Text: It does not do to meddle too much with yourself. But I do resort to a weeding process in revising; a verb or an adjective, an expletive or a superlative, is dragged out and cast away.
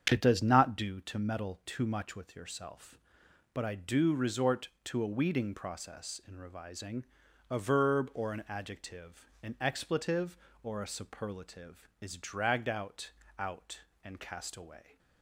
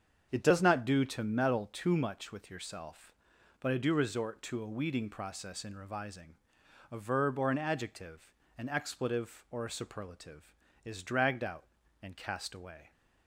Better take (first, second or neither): second